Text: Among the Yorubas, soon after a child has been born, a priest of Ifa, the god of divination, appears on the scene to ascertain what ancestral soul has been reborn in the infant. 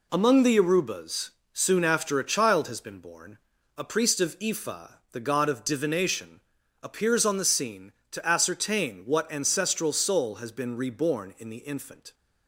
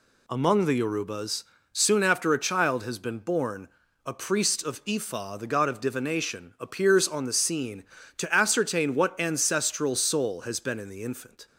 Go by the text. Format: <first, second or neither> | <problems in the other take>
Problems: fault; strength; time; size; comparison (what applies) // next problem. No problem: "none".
first | skips "reborn"; at 10.8 s